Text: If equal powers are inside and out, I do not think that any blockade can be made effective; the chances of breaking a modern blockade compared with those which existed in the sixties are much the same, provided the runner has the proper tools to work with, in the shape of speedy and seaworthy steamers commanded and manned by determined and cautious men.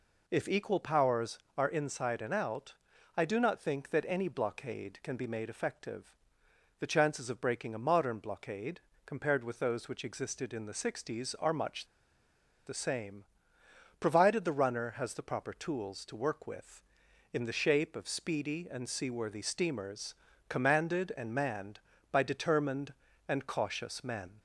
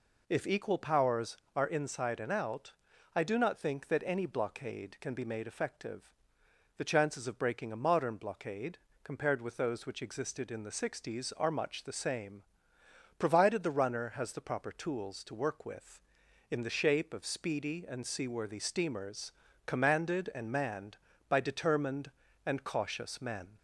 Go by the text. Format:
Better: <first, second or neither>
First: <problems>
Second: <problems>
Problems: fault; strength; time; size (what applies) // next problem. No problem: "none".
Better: second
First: pauses between "blockade" and "compared"; slight; at 8.8 s; 0.24 s long // pauses between "much" and "the"; noticeable; at 11.8 s; 0.81 s long // pauses between "steamers" and "commanded"; slight; at 20.1 s; 0.32 s long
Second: pauses between "blockade" and "compared"; slight; at 8.7 s; 0.24 s long // pauses between "steamers" and "commanded"; slight; at 19.3 s; 0.32 s long